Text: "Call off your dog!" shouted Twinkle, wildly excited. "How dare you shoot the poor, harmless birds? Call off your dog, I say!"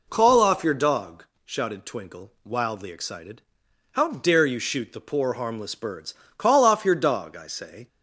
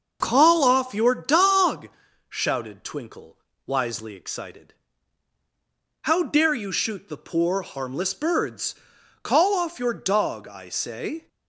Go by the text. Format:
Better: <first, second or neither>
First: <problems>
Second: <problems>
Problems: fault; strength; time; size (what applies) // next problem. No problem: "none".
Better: first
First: none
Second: starts louder than the rest; until 1.2 s; 6.5 dB // says "wisely" for "wildly"; at 3.6 s